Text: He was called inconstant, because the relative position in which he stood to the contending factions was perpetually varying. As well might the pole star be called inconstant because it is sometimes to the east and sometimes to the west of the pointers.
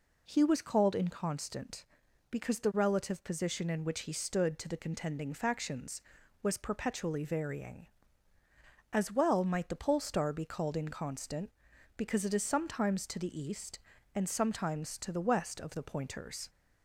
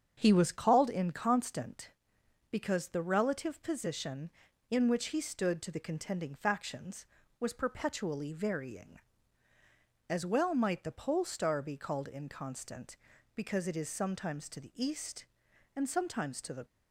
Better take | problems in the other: first | starts louder than the rest; strong; until 1.1 s; 7.5 dB // stops before "west of the pointers"; at 16.6 s

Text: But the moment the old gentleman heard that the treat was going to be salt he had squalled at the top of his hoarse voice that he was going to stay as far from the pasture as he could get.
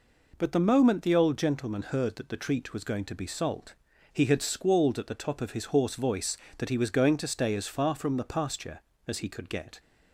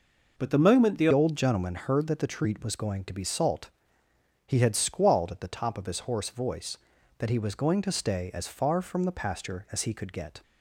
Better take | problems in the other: first | changes voice at "old"; from 1.1 s on; 9.3 s long // pauses between "salt" and "he"; noticeable; at 3.6 s; 0.78 s long; also in the first

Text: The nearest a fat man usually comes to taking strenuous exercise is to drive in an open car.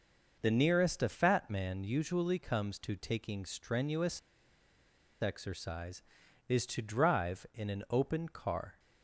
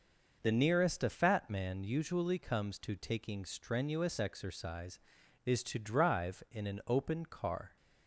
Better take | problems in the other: second | pauses between "strenuous" and "exercise"; at 4.1 s; 1.0 s long

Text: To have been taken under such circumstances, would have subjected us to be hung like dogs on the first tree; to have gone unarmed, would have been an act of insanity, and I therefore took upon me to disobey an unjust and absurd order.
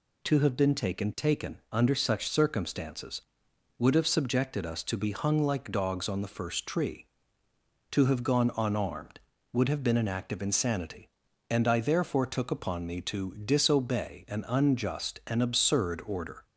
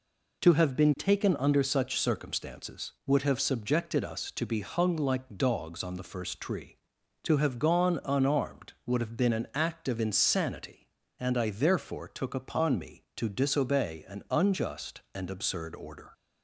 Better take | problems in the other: second | says "taken" twice; at 1.1 s

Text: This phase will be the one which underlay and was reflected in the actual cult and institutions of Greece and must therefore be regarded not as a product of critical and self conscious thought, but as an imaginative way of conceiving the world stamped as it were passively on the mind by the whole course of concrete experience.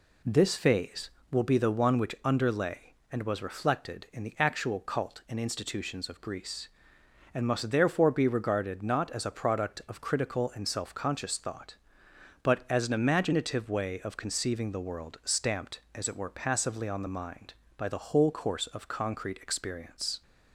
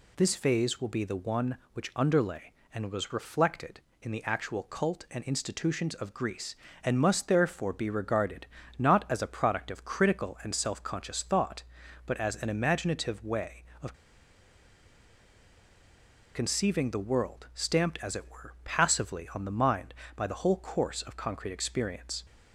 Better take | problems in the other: first | pauses between "regarded" and "not"; slight; at 8.4 s; 0.30 s long // pauses between "of" and "conceiving"; strong; at 13.9 s; 2.4 s long

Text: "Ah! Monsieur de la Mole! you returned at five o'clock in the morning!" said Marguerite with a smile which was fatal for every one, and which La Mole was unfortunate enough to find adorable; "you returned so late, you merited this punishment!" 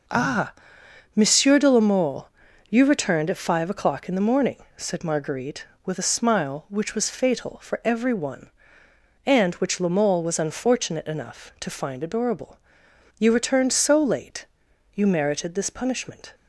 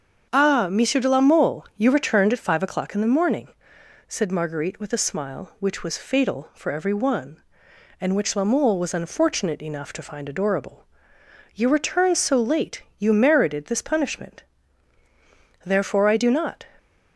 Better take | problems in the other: first | starts louder than the rest; until 1.3 s; 7 dB // goes on to say "Therefore I do not"; noticeable; from 15.6 s on; 1.0 s long

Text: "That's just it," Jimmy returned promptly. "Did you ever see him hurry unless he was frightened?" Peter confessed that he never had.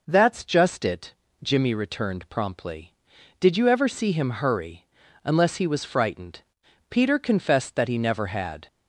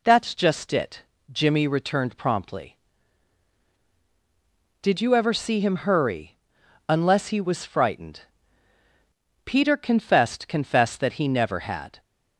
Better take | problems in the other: first | pauses between "hurry" and "unless"; noticeable; at 6.3 s; 0.52 s long; also in the first // says "confessed" twice; at 10.4 s

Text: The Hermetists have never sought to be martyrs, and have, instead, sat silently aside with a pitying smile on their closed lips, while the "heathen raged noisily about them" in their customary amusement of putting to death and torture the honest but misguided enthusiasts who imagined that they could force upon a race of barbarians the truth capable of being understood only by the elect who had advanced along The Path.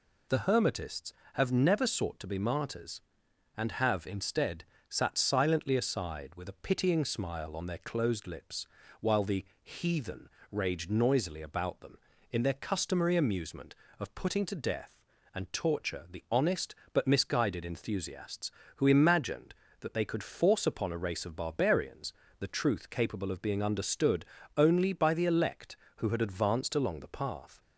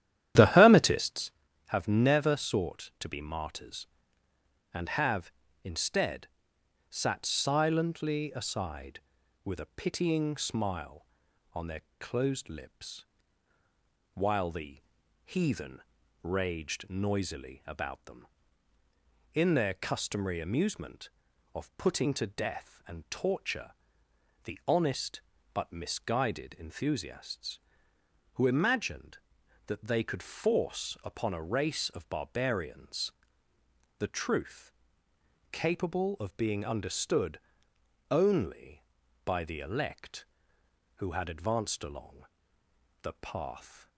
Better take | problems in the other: first | starts louder than the rest; strong; until 1.4 s; 11.5 dB // pauses between "their" and "closed"; slight; at 11.8 s; 0.20 s long // pauses between "the" and "heathen"; at 14.8 s; 0.42 s long; slight in the first // pauses between "heathen" and "raged"; at 15.8 s; 0.42 s long; slight in the first // pauses between "torture" and "the"; noticeable; at 23.7 s; 0.74 s long // pauses between "barbarians" and "the"; noticeable; at 33.1 s; 0.88 s long; slight in the first // pauses between "truth" and "capable"; noticeable; at 34.7 s; 0.80 s long // pauses between "understood" and "only"; noticeable; at 37.4 s; 0.68 s long; slight in the first // pauses between "along" and "The"; noticeable; at 42.2 s; 0.76 s long

